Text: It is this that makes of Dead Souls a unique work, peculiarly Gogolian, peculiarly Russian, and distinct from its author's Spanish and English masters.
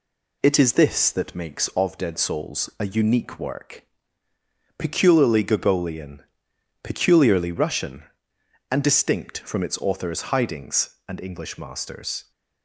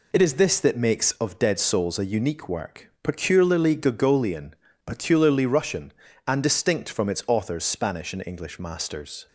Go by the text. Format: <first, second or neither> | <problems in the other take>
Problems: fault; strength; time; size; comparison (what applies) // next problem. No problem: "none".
second | says "Hidings" for "Spanish"; at 10.3 s